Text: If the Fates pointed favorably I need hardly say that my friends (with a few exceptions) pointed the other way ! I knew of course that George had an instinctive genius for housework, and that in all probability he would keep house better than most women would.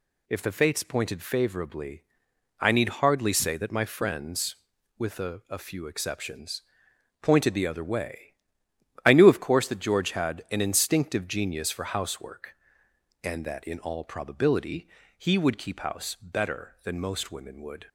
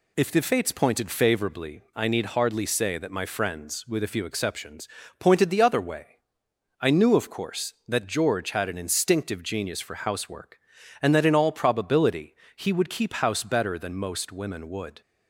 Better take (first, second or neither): second